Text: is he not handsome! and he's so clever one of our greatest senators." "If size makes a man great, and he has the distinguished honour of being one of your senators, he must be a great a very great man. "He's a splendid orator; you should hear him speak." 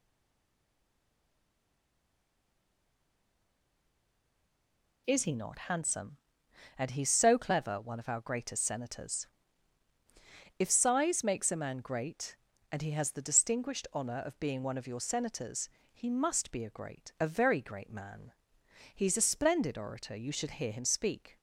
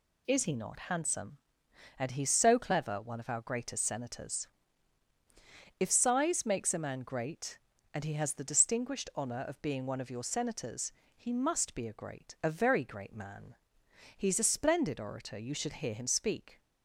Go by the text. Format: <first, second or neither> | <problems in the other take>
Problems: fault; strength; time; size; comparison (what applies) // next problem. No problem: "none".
second | stays silent before the first word; strong; until 5.0 s; 5.0 s long